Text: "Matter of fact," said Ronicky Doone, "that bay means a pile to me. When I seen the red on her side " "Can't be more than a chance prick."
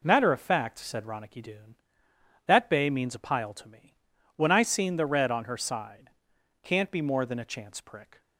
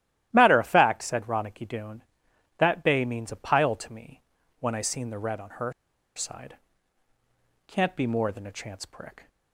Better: first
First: none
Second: starts louder than the rest; strong; until 1.3 s; 14 dB // pauses between "her" and "side"; at 5.7 s; 0.43 s long

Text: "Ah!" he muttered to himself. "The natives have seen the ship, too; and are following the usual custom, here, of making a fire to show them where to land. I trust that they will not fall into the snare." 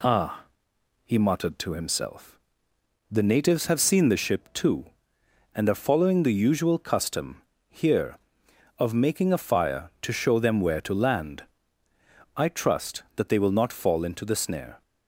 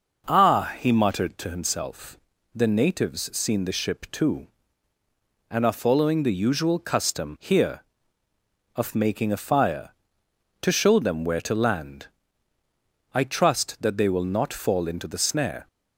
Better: first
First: none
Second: skips "have"; at 3.3 s

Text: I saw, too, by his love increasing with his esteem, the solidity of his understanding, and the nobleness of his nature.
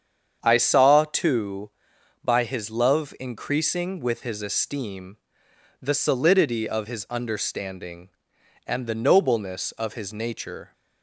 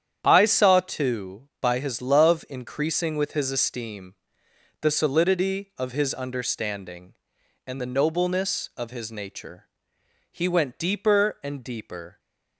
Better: first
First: starts louder than the rest; strong; until 1.4 s; 7.5 dB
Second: starts louder than the rest; strong; until 1.2 s; 9 dB // goes on to say "He went deeper and deeper"; strong; from 10.3 s on; 1.8 s long

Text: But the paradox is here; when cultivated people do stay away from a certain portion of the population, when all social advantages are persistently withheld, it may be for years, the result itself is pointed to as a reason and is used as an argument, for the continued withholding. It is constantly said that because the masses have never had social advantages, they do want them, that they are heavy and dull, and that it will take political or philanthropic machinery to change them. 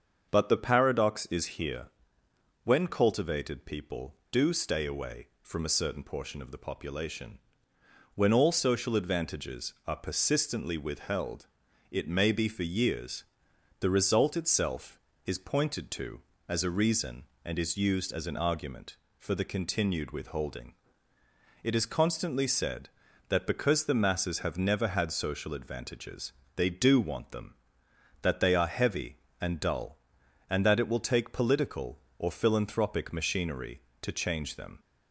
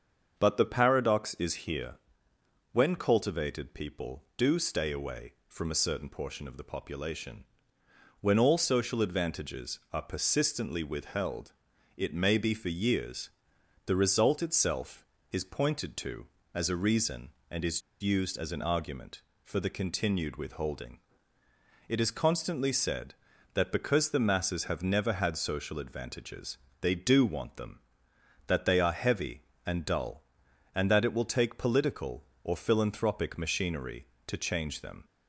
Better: first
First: starts louder than the rest; until 1.3 s; 7 dB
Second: starts louder than the rest; until 1.4 s; 7 dB // pauses between "is" and "used"; slight; at 17.8 s; 0.20 s long

